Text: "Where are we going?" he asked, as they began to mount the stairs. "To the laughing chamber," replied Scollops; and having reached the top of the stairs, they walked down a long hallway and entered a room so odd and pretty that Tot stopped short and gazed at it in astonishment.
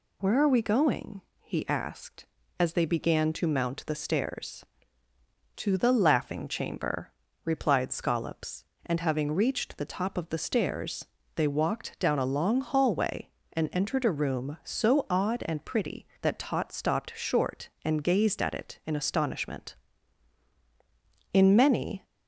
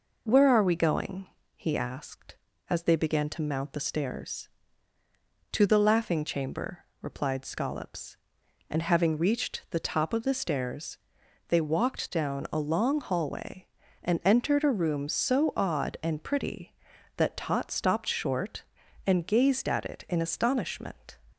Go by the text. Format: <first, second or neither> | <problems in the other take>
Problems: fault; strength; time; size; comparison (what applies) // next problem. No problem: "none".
second | goes on to say "In many"; noticeable; from 21.3 s on; 0.72 s long